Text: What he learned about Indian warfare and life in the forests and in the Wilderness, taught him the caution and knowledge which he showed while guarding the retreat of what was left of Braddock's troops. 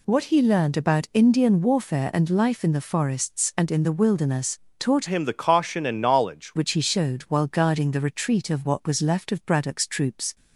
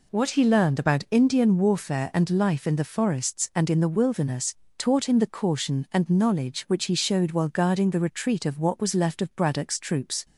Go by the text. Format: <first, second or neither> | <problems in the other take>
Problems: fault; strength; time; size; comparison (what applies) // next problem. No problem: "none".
second | changes voice from "him" to "knowledge"; from 5.0 to 6.5 s; 1.5 s long